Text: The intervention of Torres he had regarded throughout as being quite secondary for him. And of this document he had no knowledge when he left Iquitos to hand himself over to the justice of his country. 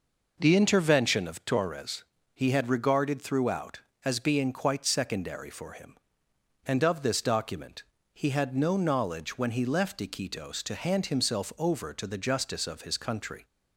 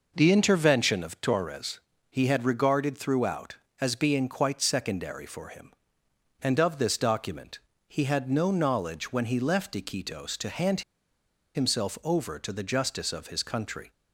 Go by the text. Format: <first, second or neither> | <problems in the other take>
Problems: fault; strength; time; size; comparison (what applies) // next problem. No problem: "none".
first | pauses between "Torres" and "he"; slight; at 1.8 s; 0.28 s long; slight in the first // pauses between "document" and "he"; slight; at 7.5 s; 0.30 s long; slight in the first // pauses between "hand" and "himself"; noticeable; at 10.8 s; 0.74 s long